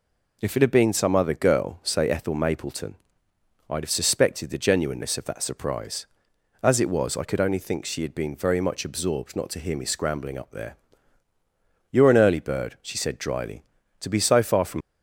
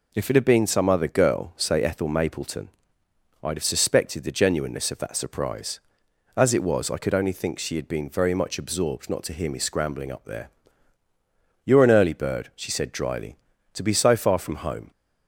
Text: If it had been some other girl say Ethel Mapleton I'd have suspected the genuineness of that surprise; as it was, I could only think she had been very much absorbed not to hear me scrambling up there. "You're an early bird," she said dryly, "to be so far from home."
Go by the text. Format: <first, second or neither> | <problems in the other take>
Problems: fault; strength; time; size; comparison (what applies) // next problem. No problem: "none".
second | pauses between "Mapleton" and "I'd"; noticeable; at 2.9 s; 0.74 s long; noticeable in the second // stops before "home"; at 14.8 s